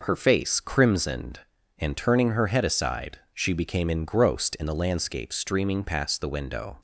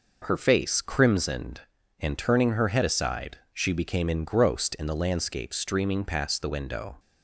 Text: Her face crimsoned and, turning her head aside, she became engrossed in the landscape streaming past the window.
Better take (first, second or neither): neither